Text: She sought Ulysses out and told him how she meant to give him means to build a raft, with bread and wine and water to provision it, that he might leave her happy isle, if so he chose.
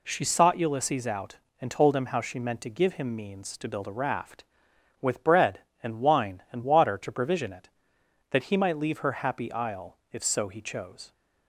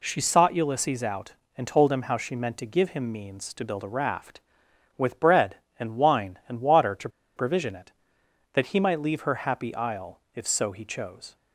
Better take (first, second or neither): first